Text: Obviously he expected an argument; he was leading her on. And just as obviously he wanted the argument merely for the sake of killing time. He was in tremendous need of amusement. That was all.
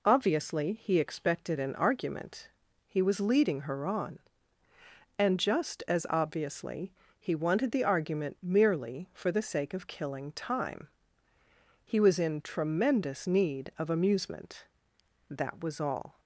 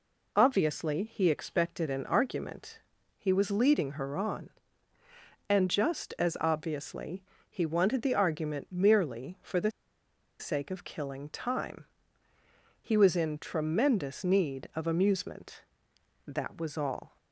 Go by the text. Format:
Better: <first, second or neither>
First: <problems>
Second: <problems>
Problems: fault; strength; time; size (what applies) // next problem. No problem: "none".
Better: first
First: pauses between "obviously" and "he"; slight; at 6.9 s; 0.28 s long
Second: pauses between "obviously" and "he"; slight; at 7.2 s; 0.28 s long // pauses between "the" and "sake"; noticeable; at 9.7 s; 0.69 s long